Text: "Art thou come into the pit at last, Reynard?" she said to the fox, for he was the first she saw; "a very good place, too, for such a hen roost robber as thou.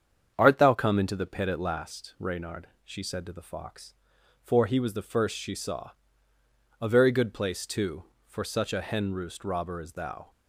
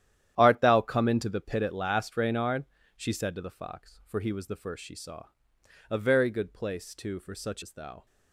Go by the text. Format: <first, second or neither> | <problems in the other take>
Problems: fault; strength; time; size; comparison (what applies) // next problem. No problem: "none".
first | starts louder than the rest; strong; until 1.3 s; 11 dB; strong in the first // skips "a hen roost robber"; at 7.6 s